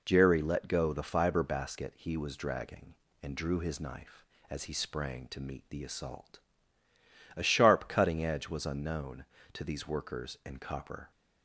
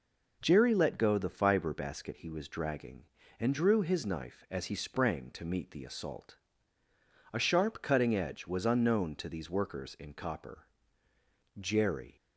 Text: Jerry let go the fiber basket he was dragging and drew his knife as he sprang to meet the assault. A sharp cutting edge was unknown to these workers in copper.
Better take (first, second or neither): first